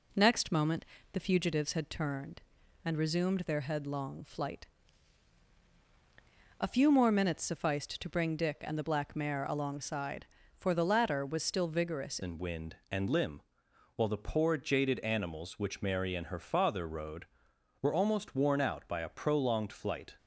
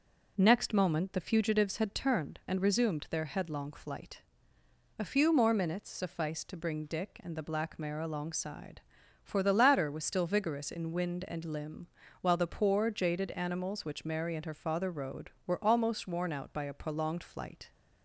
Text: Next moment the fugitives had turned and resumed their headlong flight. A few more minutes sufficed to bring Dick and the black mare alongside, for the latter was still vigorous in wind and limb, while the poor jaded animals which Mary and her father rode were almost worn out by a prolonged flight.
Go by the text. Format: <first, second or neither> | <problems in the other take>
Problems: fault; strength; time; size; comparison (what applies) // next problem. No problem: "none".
second | pauses between "moment" and "the"; slight; at 0.8 s; 0.28 s long // changes voice at "in"; from 12.2 s on; 7.9 s long